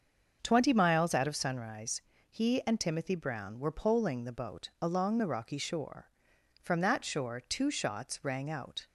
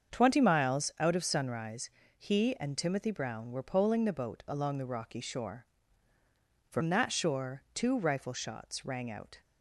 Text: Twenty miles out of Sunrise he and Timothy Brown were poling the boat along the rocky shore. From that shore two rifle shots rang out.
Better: second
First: starts louder than the rest; until 1.4 s; 6.5 dB // pauses between "Sunrise" and "he"; slight; at 1.9 s; 0.32 s long // skips "rifle"; at 7.7 s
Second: starts louder than the rest; until 1.1 s; 7 dB // pauses between "Sunrise" and "he"; slight; at 1.8 s; 0.30 s long

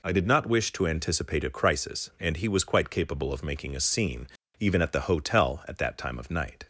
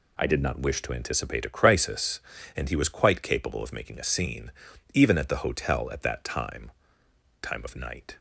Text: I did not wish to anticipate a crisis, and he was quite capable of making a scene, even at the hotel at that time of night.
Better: first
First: none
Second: says "time" twice; at 7.4 s

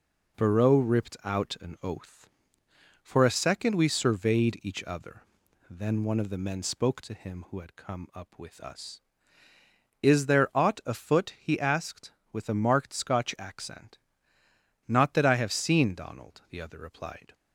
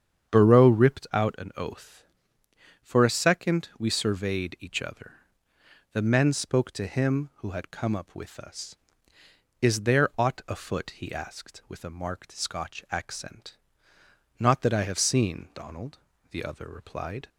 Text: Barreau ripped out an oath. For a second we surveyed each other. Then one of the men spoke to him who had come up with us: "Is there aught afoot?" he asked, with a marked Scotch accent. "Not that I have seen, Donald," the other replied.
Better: first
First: none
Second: starts louder than the rest; strong; until 1.4 s; 8 dB // skips "Then one of"; at 5.5 s

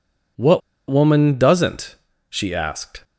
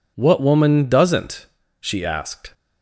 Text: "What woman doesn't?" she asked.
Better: second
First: pauses between "What" and "woman"; slight; at 0.6 s; 0.28 s long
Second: none

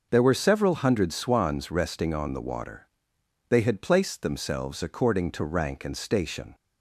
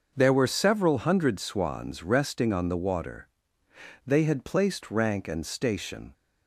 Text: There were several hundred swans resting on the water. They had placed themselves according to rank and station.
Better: first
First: none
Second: starts louder than the rest; until 1.1 s; 6 dB // skips "themselves according to"; at 4.9 s

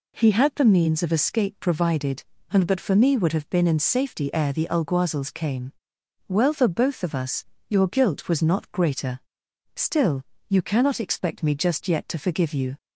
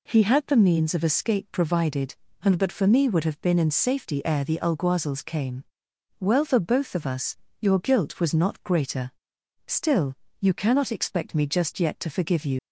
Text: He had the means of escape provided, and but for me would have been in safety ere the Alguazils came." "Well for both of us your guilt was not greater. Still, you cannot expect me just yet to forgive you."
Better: first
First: pauses between "us" and "your"; slight; at 7.4 s; 0.22 s long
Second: pauses between "us" and "your"; slight; at 7.3 s; 0.22 s long // leaves "you" unfinished; at 12.5 s; 95 ms

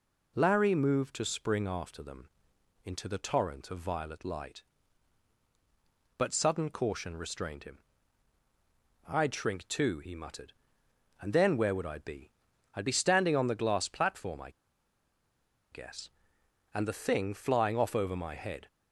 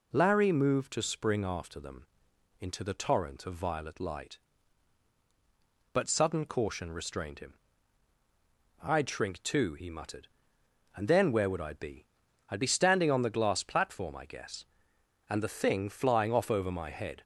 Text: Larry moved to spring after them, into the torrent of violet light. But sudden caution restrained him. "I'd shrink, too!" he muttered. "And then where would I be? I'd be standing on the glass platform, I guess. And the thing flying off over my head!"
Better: second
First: pauses between "I" and "guess"; at 14.4 s; 1.2 s long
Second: none

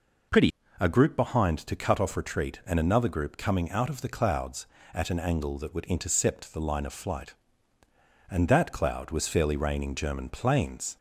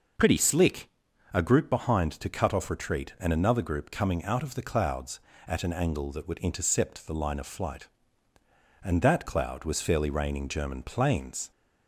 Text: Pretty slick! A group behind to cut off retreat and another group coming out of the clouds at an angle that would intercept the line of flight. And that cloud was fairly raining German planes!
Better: second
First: skips "slick"; at 0.6 s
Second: none

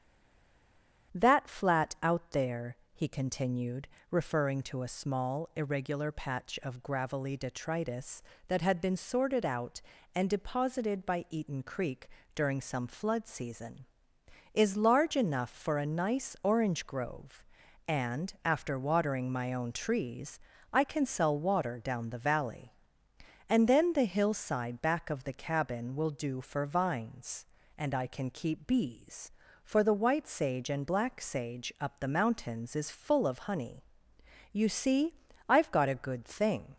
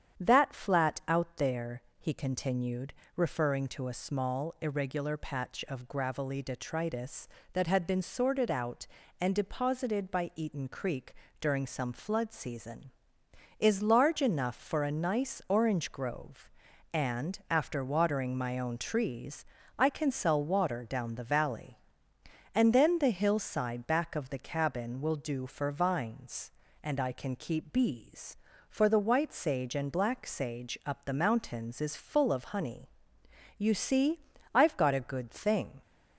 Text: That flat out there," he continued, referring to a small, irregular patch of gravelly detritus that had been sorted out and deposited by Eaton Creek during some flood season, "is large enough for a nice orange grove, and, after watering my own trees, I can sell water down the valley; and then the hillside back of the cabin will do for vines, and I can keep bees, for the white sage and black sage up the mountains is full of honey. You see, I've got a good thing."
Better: second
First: stays silent before the first word; until 1.1 s; 1.1 s long // starts louder than the rest; strong; until 2.2 s; 8.5 dB // pauses between "Creek" and "during"; slight; at 12.0 s; 0.28 s long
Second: starts louder than the rest; strong; until 1.2 s; 8.5 dB // pauses between "Creek" and "during"; slight; at 11.1 s; 0.28 s long

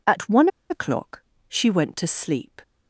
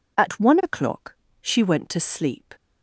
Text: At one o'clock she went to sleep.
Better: second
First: pauses between "one" and "o'clock"; slight; at 0.4 s; 0.22 s long // pauses between "o'clock" and "she"; slight; at 1.2 s; 0.26 s long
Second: pauses between "o'clock" and "she"; slight; at 1.1 s; 0.26 s long

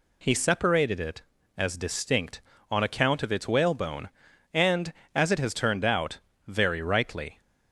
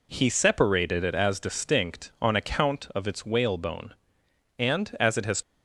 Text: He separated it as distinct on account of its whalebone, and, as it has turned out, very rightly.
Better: first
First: none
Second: stops before "turned out very rightly"; at 5.4 s

